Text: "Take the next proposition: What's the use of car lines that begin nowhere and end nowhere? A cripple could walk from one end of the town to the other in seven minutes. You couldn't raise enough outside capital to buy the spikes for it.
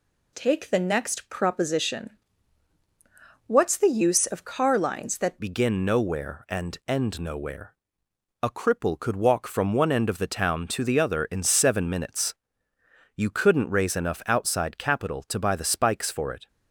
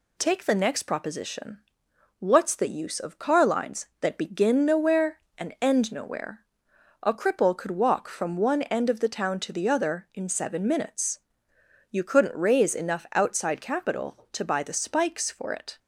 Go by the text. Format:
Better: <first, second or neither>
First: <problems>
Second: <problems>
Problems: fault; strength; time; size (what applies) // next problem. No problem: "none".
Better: second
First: changes voice at "begin"; from 5.3 s on; 11.1 s long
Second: none